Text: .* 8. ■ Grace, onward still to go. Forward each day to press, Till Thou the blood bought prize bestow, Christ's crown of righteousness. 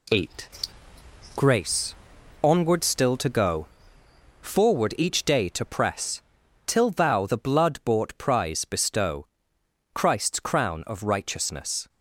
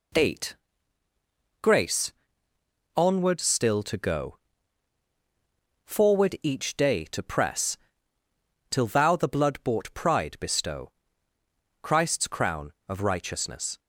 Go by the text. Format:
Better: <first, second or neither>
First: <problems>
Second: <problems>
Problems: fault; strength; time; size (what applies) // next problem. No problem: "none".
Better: first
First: none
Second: says "pride" for "prize"; at 9.9 s